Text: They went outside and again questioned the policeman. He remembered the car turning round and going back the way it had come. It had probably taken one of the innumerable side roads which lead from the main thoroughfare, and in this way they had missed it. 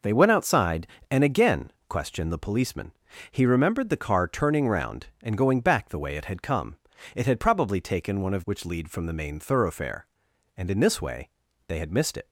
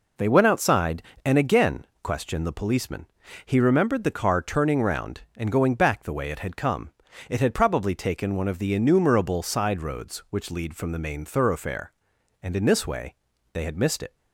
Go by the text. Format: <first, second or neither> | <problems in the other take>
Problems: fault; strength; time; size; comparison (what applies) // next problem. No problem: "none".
second | pauses between "again" and "questioned"; slight; at 1.7 s; 0.18 s long; slight in the second // skips "the innumerable side roads"; at 8.4 s // pauses between "way" and "they"; at 11.2 s; 0.38 s long; also in the second